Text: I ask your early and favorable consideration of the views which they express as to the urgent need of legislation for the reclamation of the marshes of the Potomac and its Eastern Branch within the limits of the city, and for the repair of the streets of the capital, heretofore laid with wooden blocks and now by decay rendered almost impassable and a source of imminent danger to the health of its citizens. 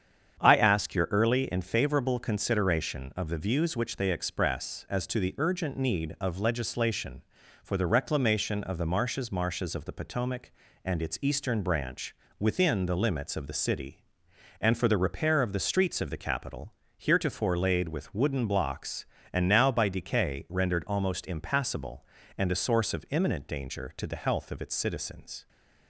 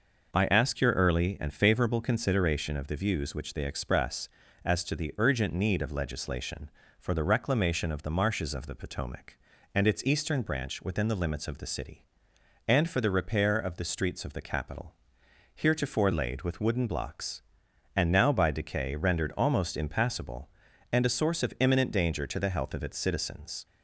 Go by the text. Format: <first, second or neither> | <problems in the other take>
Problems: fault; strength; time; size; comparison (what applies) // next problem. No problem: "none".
second | starts louder than the rest; strong; until 1.4 s; 8 dB // says "marshes" twice; at 9.3 s // pauses between "Branch" and "within"; slight; at 12.1 s; 0.24 s long